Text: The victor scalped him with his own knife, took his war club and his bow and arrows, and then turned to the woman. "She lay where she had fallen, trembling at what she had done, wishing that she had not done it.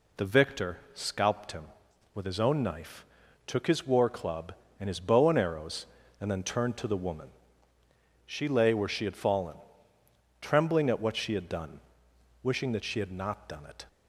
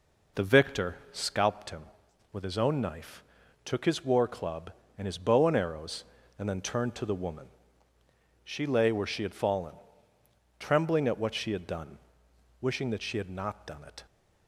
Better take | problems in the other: first | starts louder than the rest; noticeable; until 1.6 s; 4.5 dB // pauses between "victor" and "scalped"; slight; at 0.9 s; 0.16 s long; slight in the first

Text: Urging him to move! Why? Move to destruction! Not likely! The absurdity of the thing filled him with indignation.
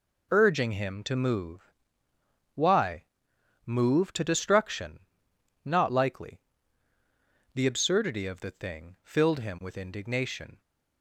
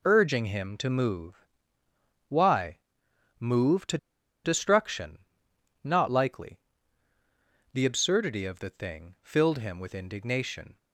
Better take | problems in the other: first | pauses between "to" and "destruction"; noticeable; at 3.9 s; 0.48 s long

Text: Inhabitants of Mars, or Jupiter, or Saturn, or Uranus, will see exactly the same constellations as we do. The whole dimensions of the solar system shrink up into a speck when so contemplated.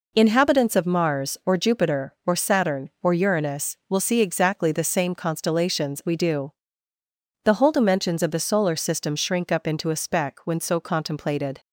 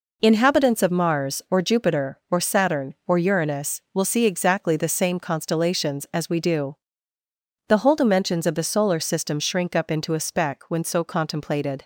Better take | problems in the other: second | skips "as"; at 6.0 s

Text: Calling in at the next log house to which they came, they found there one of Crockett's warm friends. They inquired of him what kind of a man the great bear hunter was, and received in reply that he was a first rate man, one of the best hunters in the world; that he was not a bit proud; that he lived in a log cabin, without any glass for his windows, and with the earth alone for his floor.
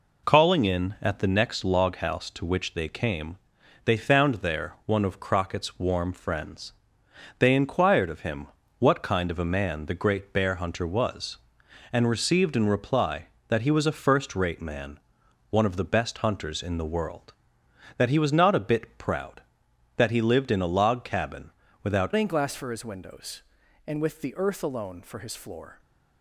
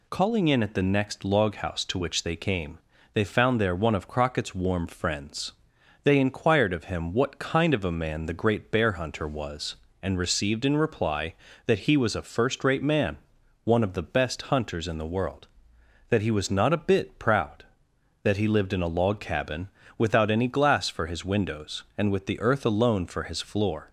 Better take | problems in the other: second | pauses between "him" and "what"; slight; at 8.4 s; 0.32 s long // changes voice at "any"; from 22.1 s on; 3.6 s long

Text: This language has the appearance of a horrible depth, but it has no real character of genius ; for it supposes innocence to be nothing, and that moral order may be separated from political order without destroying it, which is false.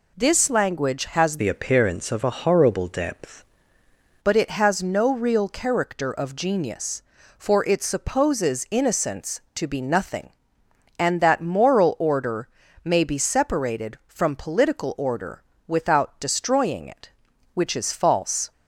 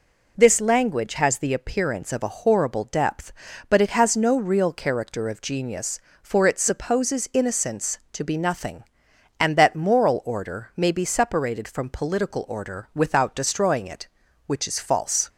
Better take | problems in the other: second | changes voice from "the" to "depth"; from 1.3 to 3.4 s; 2.1 s long // pauses between "order" and "may"; at 12.4 s; 0.38 s long // pauses between "order" and "without"; slight; at 15.4 s; 0.24 s long

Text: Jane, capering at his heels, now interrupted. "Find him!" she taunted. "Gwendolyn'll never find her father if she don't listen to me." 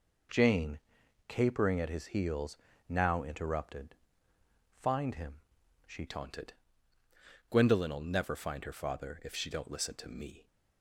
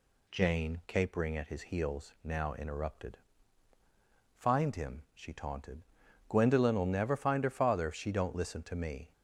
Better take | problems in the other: second | changes voice at "taunted"; from 6.0 s on; 4.4 s long

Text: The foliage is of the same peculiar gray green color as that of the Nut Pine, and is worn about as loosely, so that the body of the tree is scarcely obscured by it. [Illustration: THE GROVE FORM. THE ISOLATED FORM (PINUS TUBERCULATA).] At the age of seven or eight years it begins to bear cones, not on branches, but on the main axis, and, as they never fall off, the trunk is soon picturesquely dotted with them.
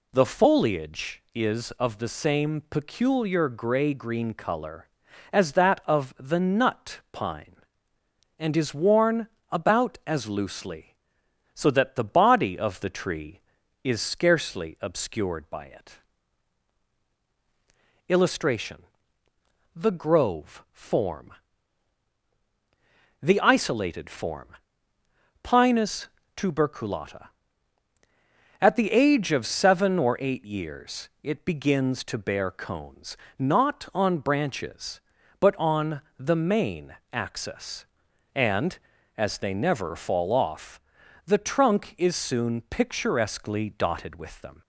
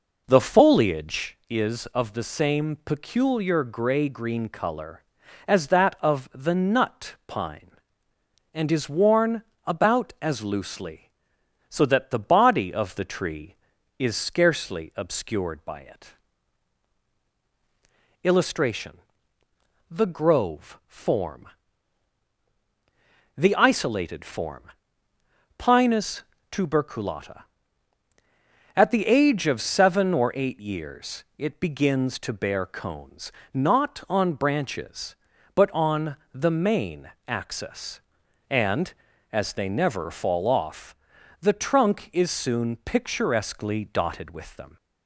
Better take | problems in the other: first | starts louder than the rest; noticeable; until 1.4 s; 4.5 dB // pauses between "worn" and "about"; slight; at 9.4 s; 0.22 s long; slight in the first // pauses between "PINUS" and "TUBERCULATA"; slight; at 26.2 s; 0.28 s long; slight in the first // pauses between "on" and "the"; slight; at 36.1 s; 0.16 s long; slight in the first // pauses between "main" and "axis"; slight; at 37.1 s; 0.16 s long; slight in the first

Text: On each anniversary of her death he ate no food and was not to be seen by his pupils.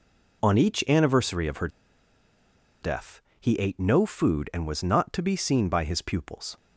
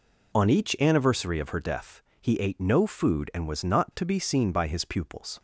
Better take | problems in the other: second | pauses between "her" and "death"; at 1.6 s; 1.1 s long // pauses between "death" and "he"; slight; at 3.2 s; 0.20 s long; slight in the second

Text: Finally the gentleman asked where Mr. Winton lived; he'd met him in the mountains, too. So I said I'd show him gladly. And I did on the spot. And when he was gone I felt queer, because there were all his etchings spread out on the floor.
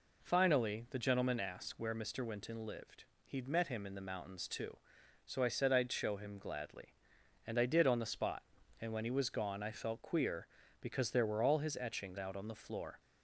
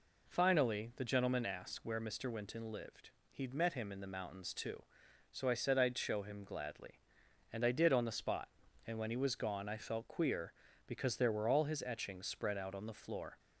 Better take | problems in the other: second | skips "spread"; at 12.1 s

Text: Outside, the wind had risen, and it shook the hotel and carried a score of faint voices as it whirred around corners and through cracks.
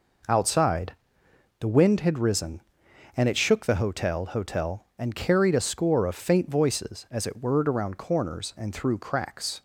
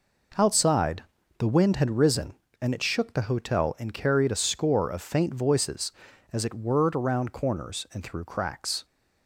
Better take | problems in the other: second | says "hotel" twice; at 4.2 s

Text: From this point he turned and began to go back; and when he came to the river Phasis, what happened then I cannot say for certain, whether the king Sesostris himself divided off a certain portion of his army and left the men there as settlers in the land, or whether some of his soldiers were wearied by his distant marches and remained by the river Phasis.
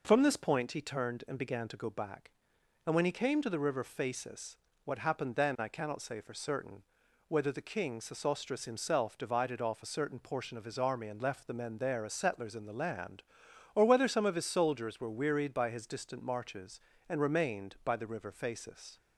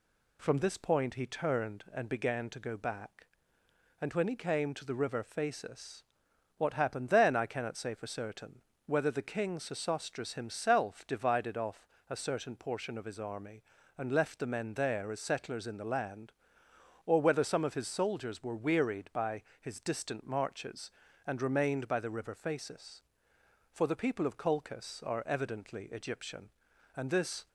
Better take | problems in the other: first | pauses between "off" and "a"; slight; at 11.8 s; 0.21 s long // pauses between "by" and "his"; slight; at 19.4 s; 0.18 s long // goes on to say "For the people of Colchis are evidently Egyptian and this"; strong; from 23.7 s on; 3.7 s long

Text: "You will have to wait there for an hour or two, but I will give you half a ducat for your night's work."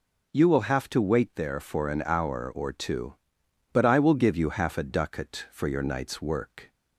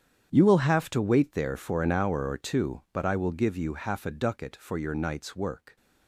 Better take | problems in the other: first | gets quieter; strong; throughout; 16.5 dB

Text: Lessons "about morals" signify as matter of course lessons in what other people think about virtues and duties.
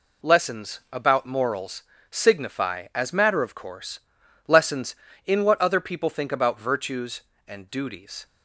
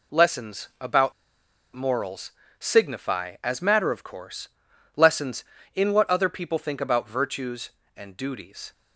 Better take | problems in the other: first | pauses between "about" and "morals"; noticeable; at 1.1 s; 0.63 s long // pauses between "morals" and "signify"; slight; at 2.3 s; 0.26 s long; slight in the first // pauses between "course" and "lessons"; noticeable; at 4.4 s; 0.48 s long; noticeable in the first

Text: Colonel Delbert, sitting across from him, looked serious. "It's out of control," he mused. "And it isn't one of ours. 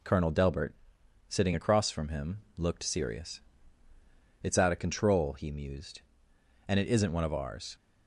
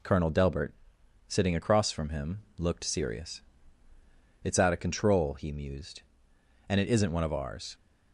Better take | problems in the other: neither | none

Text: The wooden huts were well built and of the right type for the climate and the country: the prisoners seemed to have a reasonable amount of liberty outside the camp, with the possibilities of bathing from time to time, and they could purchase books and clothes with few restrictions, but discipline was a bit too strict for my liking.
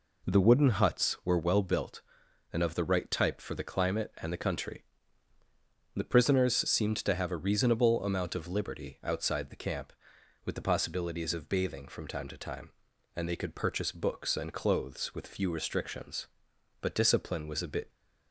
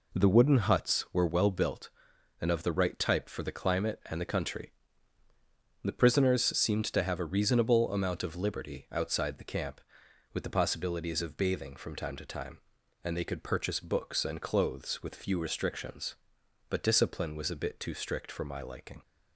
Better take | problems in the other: second | stops before "too strict for my liking"; at 17.9 s

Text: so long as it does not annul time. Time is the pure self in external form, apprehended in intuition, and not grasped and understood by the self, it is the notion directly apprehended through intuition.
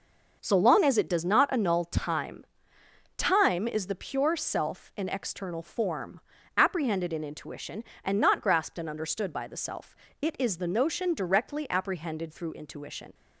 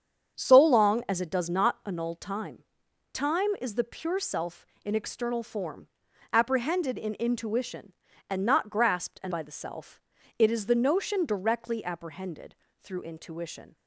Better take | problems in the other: first | starts louder than the rest; strong; until 1.4 s; 7.5 dB // skips "understood"; at 9.3 s // pauses between "apprehended" and "through"; slight; at 12.5 s; 0.26 s long

